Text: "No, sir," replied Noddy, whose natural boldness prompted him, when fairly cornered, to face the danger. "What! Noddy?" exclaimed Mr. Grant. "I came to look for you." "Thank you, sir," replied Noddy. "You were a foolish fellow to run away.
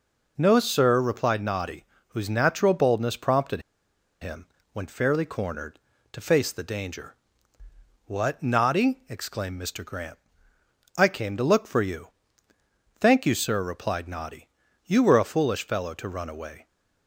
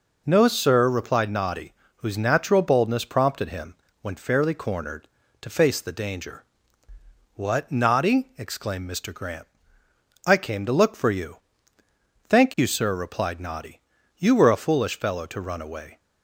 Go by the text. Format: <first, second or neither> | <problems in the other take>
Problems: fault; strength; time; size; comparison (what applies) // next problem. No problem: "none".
second | pauses between "prompted" and "him"; noticeable; at 3.6 s; 0.60 s long